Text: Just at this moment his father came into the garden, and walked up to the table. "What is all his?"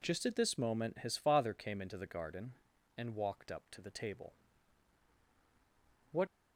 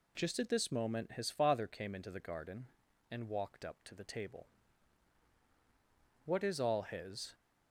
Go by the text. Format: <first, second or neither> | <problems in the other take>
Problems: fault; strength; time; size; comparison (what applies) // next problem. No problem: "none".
second | stops before "is all his"; at 6.2 s